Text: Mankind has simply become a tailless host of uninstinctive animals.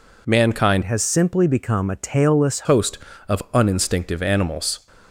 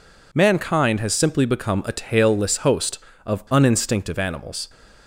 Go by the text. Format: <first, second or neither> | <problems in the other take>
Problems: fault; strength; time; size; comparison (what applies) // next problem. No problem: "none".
second | changes voice from "has" to "tailless"; from 0.8 to 2.6 s; 1.8 s long